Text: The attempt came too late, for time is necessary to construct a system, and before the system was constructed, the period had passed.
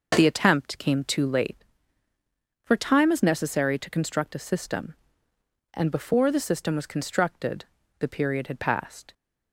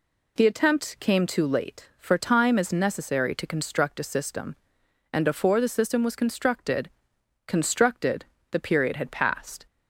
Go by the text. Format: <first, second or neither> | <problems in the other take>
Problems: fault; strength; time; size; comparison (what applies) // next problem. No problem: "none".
first | says "constructed" twice; at 7.4 s